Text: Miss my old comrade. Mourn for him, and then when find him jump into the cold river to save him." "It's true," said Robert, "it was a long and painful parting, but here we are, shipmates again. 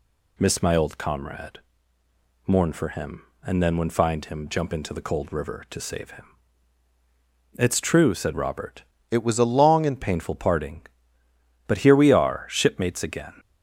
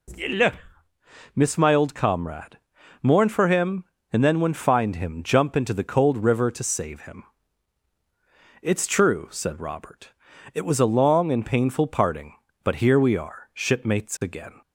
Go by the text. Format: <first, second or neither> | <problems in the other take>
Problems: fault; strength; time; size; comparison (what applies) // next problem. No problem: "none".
second | changes voice from "it" to "and"; from 9.0 to 9.9 s; 0.9 s long